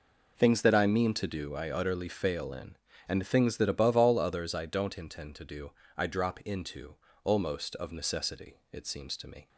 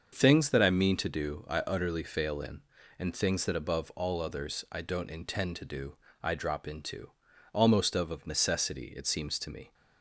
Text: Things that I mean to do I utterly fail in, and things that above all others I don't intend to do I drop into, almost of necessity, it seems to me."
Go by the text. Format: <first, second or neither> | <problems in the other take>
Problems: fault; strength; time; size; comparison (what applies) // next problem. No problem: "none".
first | starts louder than the rest; until 1.1 s; 6.5 dB // pauses between "do" and "I"; slight; at 5.9 s; 0.26 s long; slight in the first // says "of" twice; at 8.1 s